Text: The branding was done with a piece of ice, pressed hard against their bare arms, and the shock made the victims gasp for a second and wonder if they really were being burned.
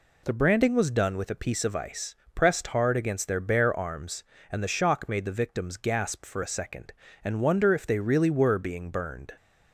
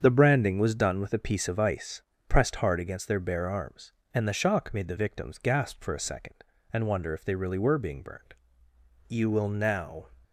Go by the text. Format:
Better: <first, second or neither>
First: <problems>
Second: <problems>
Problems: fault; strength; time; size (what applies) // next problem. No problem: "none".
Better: first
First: none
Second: starts louder than the rest; strong; until 1.0 s; 7 dB // goes on to say "You will now"; noticeable; from 9.0 s on; 0.96 s long